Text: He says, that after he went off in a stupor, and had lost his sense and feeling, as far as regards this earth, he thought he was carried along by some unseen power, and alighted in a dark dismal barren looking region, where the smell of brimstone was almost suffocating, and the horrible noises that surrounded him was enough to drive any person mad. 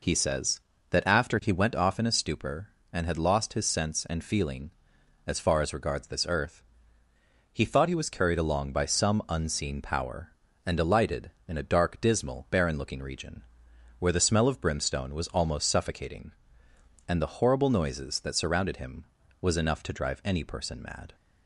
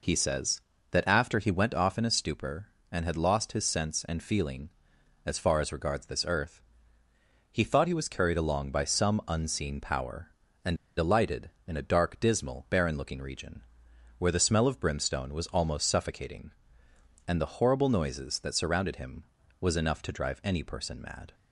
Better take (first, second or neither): first